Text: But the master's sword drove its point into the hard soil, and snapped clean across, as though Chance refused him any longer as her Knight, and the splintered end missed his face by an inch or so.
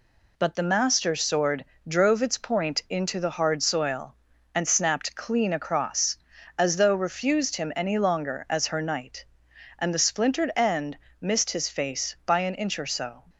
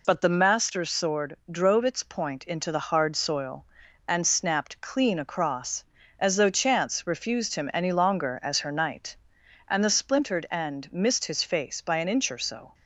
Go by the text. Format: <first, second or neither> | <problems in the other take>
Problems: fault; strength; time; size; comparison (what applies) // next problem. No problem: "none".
second | pauses between "sword" and "drove"; slight; at 1.6 s; 0.24 s long // skips "Chance"; at 6.9 s // pauses between "end" and "missed"; slight; at 10.9 s; 0.24 s long